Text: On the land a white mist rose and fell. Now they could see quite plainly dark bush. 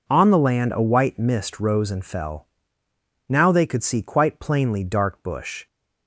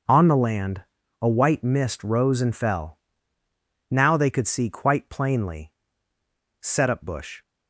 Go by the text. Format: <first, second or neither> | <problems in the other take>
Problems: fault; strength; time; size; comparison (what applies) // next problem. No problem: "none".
first | starts louder than the rest; noticeable; until 1.4 s; 6 dB // pauses between "land" and "a"; slight; at 0.8 s; 0.36 s long // says "setup" for "dark"; at 6.5 s